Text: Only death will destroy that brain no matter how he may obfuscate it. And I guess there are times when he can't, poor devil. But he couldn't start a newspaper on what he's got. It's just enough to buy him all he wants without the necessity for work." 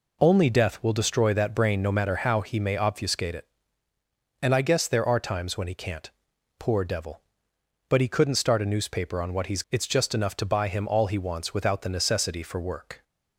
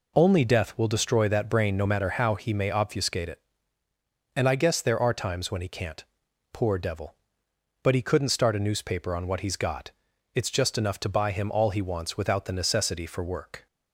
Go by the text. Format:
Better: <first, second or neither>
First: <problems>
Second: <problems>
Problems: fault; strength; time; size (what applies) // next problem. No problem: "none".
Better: second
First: skips "got"; at 9.6 s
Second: none